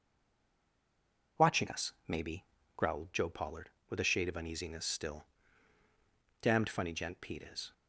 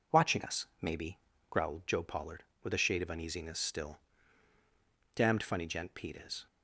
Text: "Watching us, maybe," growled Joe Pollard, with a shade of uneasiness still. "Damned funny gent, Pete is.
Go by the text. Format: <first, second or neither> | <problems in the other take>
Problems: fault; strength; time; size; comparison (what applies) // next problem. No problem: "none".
second | stays silent before the first word; noticeable; until 1.3 s; 1.3 s long